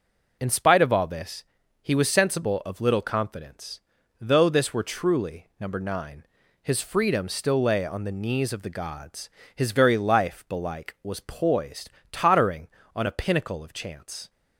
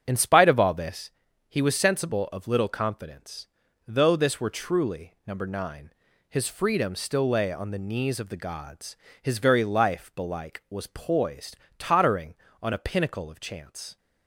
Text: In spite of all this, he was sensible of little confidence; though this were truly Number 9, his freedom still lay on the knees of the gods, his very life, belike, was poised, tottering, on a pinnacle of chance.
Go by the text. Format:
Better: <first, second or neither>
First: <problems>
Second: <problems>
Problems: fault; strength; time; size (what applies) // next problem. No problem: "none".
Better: first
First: none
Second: starts louder than the rest; strong; until 1.0 s; 8 dB